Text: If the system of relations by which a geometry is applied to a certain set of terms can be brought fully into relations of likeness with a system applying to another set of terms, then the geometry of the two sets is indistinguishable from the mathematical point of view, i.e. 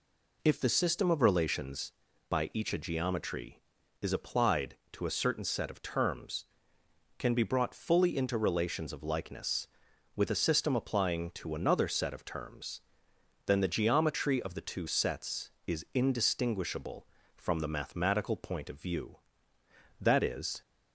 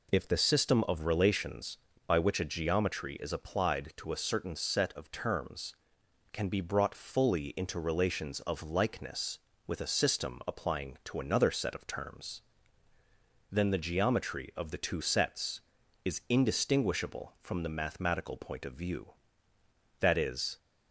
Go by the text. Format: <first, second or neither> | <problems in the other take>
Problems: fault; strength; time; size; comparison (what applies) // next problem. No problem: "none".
second | says "each" for "which"; at 2.5 s